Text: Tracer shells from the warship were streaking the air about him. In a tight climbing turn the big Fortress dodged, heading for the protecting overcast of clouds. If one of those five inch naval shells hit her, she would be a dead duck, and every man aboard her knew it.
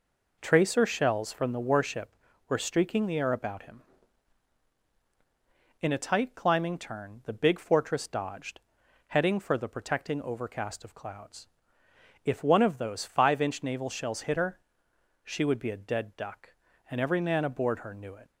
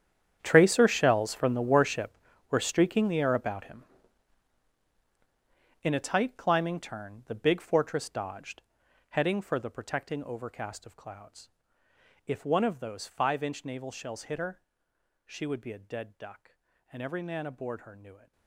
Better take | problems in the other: first | gets quieter; strong; throughout; 17.5 dB

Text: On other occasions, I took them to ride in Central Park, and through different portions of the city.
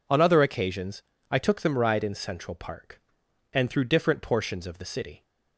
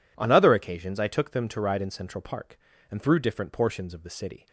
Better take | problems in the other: second | skips "to"; at 1.7 s

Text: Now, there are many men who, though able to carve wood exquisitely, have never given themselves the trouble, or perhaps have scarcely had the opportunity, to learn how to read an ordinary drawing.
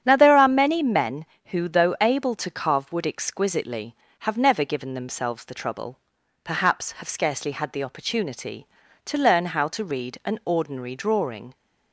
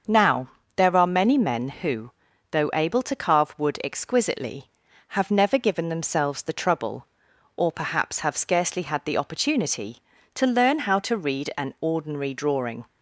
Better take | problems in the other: second | starts louder than the rest; strong; until 1.0 s; 9 dB; also in the second // skips "or"; at 6.1 s

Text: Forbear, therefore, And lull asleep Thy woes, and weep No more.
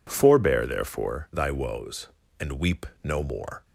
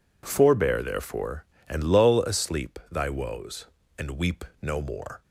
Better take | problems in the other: second | skips "And lull asleep"; at 1.3 s // pauses between "weep" and "No"; slight; at 2.8 s; 0.16 s long; slight in the second

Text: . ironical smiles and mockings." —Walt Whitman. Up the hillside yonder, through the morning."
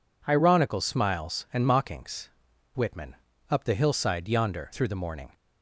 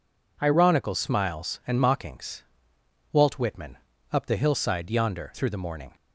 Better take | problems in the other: second | skips "Walt"; at 2.5 s

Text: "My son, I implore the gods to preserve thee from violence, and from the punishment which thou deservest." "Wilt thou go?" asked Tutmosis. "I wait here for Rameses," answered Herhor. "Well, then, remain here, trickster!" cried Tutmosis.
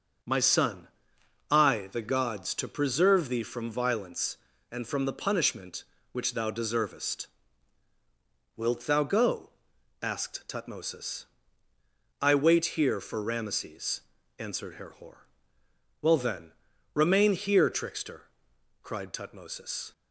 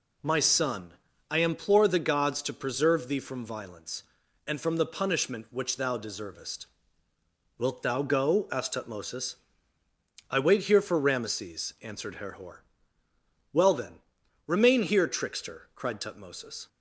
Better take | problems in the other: second | starts louder than the rest; until 1.8 s; 7 dB // skips "implore"; at 1.9 s

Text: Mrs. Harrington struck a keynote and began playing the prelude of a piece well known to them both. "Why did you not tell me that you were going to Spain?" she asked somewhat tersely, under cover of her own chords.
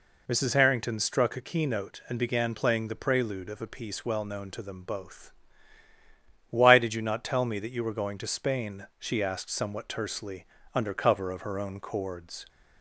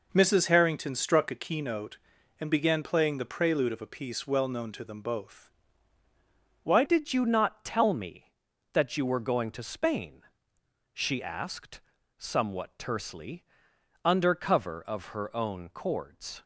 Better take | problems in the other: first | changes voice at "did"; from 6.8 s on; 9.6 s long // pauses between "asked" and "somewhat"; at 11.7 s; 0.40 s long

